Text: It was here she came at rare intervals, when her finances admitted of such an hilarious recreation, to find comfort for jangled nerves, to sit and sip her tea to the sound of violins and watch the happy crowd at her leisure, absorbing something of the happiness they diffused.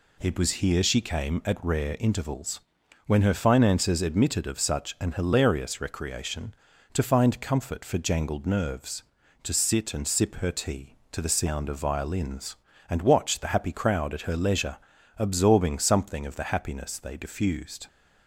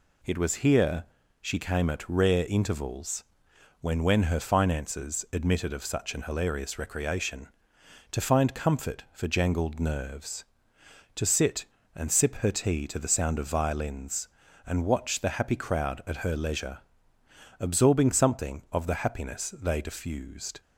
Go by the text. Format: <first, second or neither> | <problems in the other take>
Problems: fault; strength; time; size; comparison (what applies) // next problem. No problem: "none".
first | pauses between "here" and "she"; slight; at 1.0 s; 0.36 s long // says "when" twice; at 4.0 s